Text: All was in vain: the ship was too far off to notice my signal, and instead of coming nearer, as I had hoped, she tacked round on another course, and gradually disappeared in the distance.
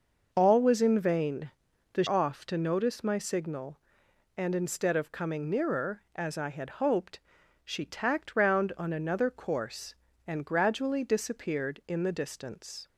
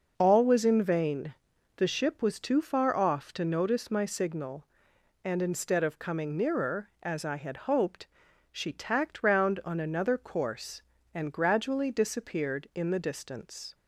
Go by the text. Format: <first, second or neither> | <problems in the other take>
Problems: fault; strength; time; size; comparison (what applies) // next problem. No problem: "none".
second | skips "ship was too far"; at 2.0 s